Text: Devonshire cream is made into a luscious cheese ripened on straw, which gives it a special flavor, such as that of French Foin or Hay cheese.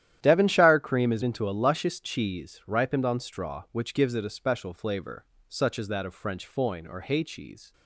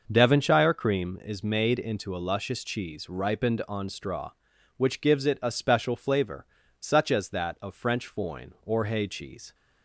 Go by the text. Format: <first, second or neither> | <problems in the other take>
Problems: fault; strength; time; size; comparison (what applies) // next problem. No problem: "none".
second | starts louder than the rest; strong; until 1.2 s; 11.5 dB // skips "made"; at 1.2 s